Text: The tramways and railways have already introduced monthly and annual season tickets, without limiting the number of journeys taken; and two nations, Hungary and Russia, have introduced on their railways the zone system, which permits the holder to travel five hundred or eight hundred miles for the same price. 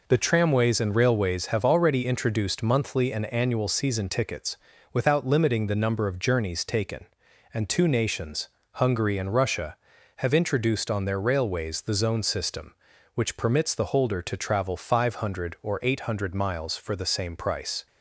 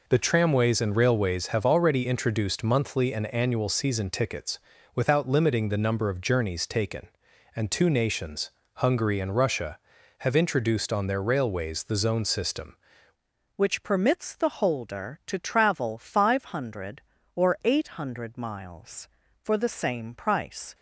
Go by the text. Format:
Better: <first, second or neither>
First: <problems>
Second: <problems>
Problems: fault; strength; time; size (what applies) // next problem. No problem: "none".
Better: first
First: none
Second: changes voice at "which"; from 13.5 s on; 7.2 s long